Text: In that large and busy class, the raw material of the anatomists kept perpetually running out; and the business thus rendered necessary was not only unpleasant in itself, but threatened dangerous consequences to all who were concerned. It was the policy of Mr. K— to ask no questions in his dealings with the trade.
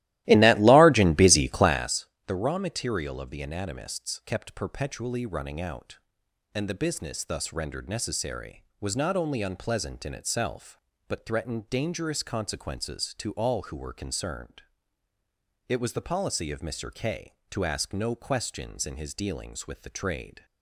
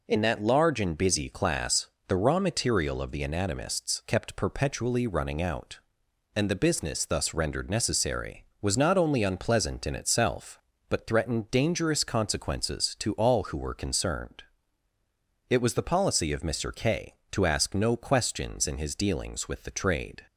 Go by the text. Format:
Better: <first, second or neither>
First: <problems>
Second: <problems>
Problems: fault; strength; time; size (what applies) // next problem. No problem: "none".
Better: second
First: starts louder than the rest; strong; until 1.9 s; 16 dB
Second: none